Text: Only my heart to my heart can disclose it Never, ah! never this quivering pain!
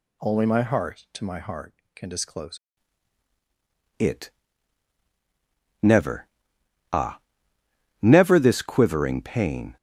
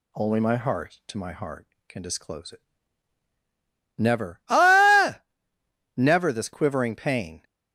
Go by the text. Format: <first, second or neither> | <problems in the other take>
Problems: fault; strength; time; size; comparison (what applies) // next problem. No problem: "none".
second | changes voice at "it"; from 4.0 s on; 5.7 s long // pauses between "it" and "Never"; strong; at 4.3 s; 1.5 s long; strong in the second